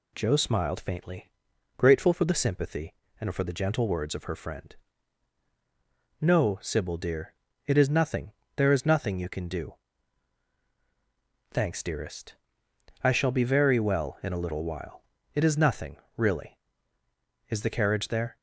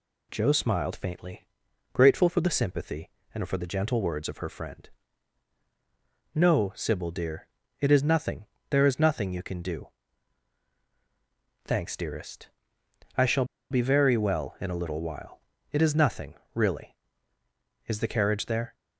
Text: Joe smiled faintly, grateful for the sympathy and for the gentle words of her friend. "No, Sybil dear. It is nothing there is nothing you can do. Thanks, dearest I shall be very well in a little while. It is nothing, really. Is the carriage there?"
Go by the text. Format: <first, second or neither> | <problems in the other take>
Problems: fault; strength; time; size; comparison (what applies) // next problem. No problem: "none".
first | pauses between "nothing" and "there"; slight; at 8.4 s; 0.24 s long; slight in the first // pauses between "dearest" and "I"; noticeable; at 12.4 s; 0.70 s long; noticeable in the first // pauses between "shall" and "be"; slight; at 13.4 s; 0.26 s long